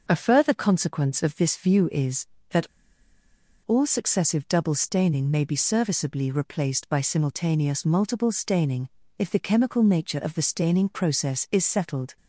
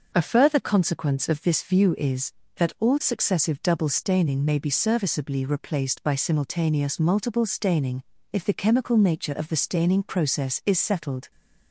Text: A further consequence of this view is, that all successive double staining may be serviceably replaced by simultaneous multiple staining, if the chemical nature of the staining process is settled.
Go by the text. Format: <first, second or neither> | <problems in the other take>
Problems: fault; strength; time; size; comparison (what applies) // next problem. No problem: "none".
second | starts louder than the rest; noticeable; until 1.0 s; 6 dB; noticeable in the second // pauses between "that" and "all"; noticeable; at 2.6 s; 0.97 s long